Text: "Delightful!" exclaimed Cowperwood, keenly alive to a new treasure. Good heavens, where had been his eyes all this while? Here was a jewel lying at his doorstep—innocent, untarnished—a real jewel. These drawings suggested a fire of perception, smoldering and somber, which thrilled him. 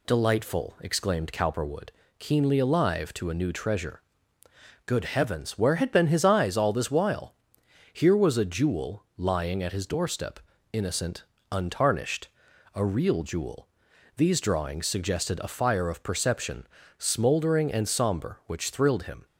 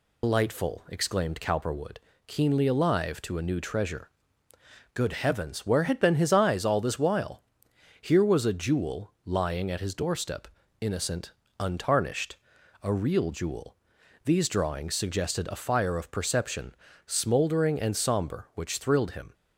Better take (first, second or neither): first